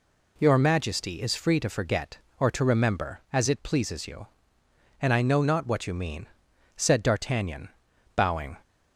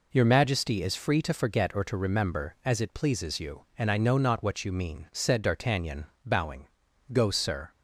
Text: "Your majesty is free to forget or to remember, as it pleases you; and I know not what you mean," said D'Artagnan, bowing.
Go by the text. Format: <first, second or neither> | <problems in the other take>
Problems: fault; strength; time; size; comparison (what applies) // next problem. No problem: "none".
first | goes on to say "Go sir"; from 7.1 s on; 0.58 s long